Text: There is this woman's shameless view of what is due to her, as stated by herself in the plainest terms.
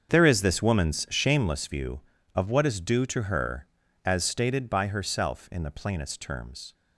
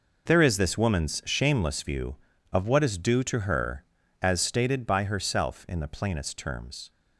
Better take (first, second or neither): second